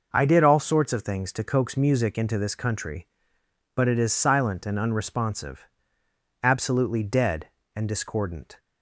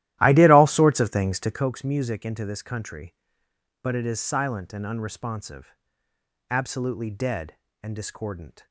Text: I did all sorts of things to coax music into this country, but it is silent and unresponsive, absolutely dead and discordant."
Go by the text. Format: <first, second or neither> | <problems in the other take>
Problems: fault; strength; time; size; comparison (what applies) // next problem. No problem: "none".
first | starts louder than the rest; strong; until 1.7 s; 14.5 dB